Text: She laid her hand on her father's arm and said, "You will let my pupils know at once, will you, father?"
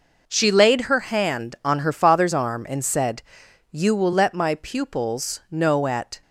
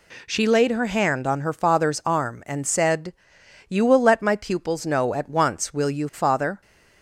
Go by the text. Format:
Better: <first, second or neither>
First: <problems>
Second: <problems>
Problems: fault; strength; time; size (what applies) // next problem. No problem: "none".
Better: second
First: stops before "once will you father"; at 6.2 s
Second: none